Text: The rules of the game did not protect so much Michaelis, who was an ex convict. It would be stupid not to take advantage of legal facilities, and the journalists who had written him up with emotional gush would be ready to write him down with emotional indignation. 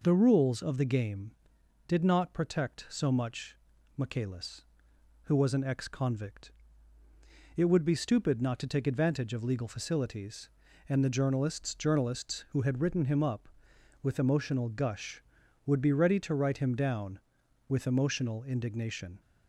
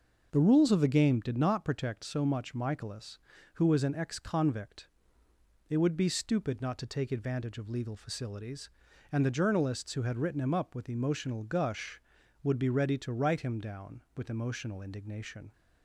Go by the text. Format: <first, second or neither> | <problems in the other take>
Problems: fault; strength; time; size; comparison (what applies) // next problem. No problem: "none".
second | pauses between "much" and "Michaelis"; at 3.5 s; 0.42 s long // says "journalists" twice; at 11.7 s